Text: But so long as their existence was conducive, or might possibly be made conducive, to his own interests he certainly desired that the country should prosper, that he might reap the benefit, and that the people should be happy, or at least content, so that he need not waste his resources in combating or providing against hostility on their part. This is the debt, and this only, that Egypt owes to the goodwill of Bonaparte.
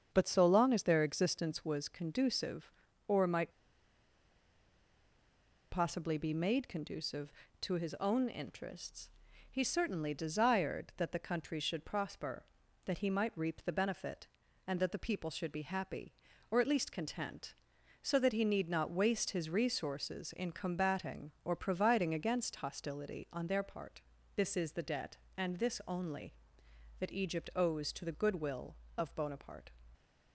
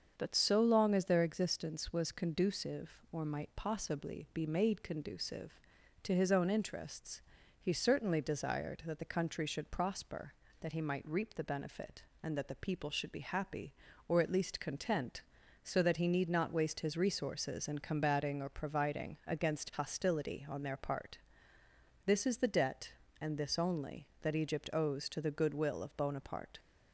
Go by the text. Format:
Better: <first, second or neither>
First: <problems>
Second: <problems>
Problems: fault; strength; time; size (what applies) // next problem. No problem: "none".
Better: second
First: starts louder than the rest; strong; until 1.1 s; 7.5 dB // pauses between "might" and "possibly"; strong; at 3.5 s; 2.1 s long // pauses between "interests" and "he"; at 9.0 s; 0.44 s long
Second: starts louder than the rest; until 1.1 s; 7 dB // pauses between "interests" and "he"; at 7.2 s; 0.38 s long